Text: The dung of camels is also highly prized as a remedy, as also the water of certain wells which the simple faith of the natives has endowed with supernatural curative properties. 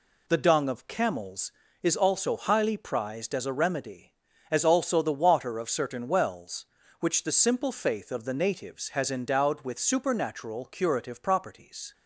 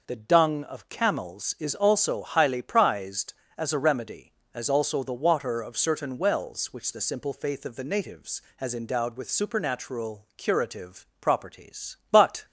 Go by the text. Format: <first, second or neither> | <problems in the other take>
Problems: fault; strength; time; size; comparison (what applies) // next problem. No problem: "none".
first | goes on to say "But"; slight; from 12.1 s on; 0.34 s long